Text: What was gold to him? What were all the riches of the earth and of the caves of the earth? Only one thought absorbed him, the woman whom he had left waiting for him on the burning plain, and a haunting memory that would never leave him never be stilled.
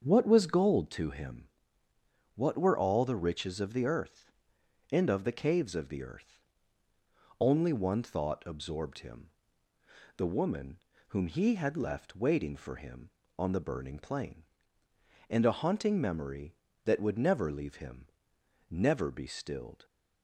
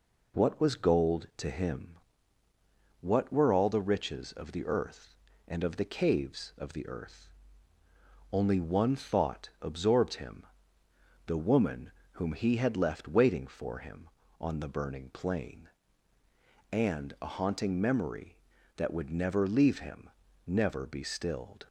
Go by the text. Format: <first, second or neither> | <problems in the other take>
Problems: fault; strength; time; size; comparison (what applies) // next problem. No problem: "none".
second | starts louder than the rest; until 0.9 s; 7 dB // pauses between "woman" and "whom"; slight; at 10.7 s; 0.30 s long; slight in the second // pauses between "him" and "never"; noticeable; at 18.0 s; 0.62 s long; slight in the second